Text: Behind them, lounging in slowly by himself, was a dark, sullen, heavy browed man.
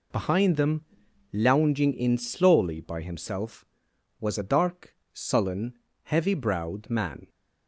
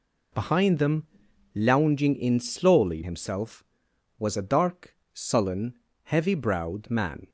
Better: first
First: none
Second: skips "by"; at 3.0 s

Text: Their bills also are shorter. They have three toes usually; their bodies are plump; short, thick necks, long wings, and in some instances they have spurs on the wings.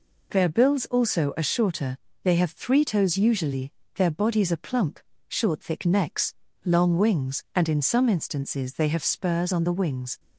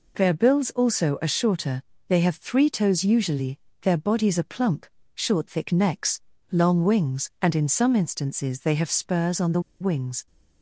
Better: first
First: none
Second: pauses between "the" and "wings"; slight; at 9.5 s; 0.20 s long

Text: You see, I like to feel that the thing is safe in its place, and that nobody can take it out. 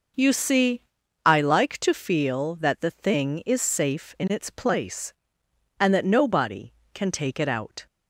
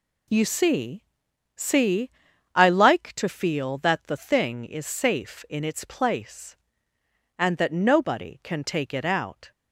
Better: first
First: none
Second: says "see" twice; at 1.5 s

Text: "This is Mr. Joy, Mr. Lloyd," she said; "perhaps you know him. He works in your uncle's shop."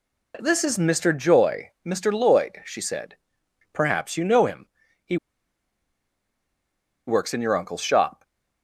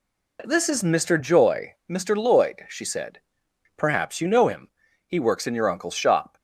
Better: second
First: pauses between "He" and "works"; strong; at 5.1 s; 1.9 s long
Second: none

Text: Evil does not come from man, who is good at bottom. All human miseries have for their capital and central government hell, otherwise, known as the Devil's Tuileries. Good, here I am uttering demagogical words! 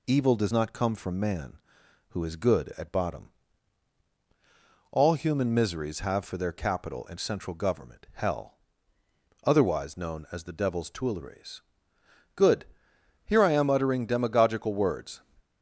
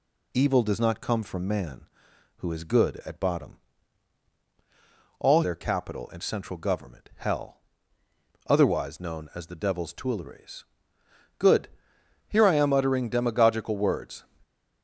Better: first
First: none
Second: skips "human miseries have for"; at 5.4 s

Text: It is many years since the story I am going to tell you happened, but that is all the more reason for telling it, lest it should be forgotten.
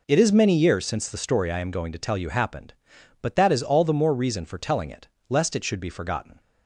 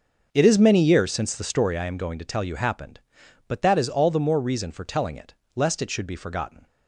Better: first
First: none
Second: starts louder than the rest; until 1.8 s; 6 dB

